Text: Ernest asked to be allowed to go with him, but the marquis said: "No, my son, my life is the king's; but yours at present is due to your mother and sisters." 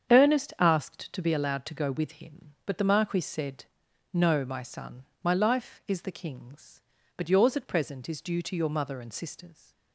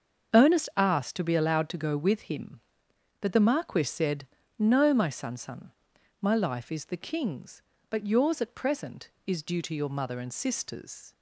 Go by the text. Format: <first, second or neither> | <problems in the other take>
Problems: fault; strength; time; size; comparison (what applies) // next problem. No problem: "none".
first | starts louder than the rest; until 1.4 s; 7 dB; strong in the first // says "son" twice; at 5.3 s